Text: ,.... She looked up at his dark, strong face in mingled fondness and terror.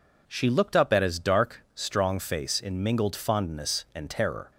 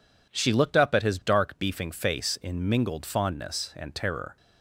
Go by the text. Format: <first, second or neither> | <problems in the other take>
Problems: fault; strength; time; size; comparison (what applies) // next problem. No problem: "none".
first | says "beefing" for "strong"; at 1.5 s